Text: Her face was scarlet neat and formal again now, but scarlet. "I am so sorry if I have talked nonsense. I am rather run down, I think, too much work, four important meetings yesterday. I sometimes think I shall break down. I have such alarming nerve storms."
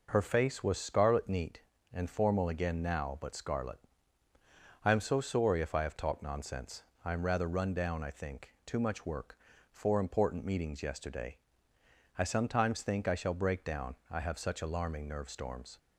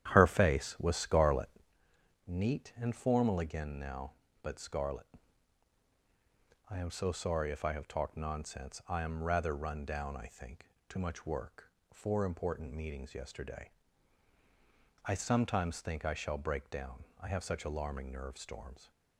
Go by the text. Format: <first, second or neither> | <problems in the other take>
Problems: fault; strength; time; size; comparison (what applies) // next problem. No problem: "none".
first | starts louder than the rest; strong; until 1.8 s; 10.5 dB // pauses between "scarlet" and "neat"; noticeable; at 1.4 s; 0.78 s long